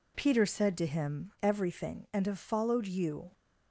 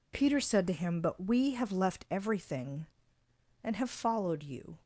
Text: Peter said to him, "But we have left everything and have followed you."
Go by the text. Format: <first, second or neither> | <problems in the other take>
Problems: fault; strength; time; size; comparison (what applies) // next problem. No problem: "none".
second | skips "But we have left"; at 1.3 s